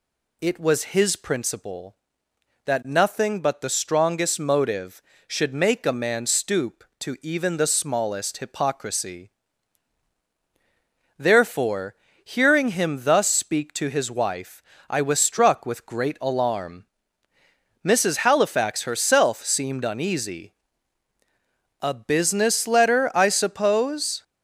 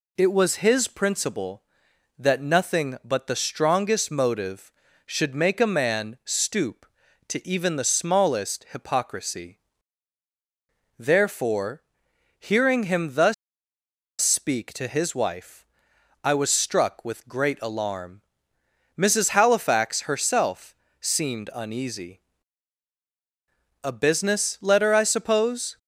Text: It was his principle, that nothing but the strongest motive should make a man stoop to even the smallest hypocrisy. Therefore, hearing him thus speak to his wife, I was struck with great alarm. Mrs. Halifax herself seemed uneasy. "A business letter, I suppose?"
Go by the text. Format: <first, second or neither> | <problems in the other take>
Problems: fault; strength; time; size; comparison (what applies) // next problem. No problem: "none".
first | pauses between "thus" and "speak"; noticeable; at 13.3 s; 0.87 s long // pauses between "herself" and "seemed"; slight; at 20.7 s; 0.24 s long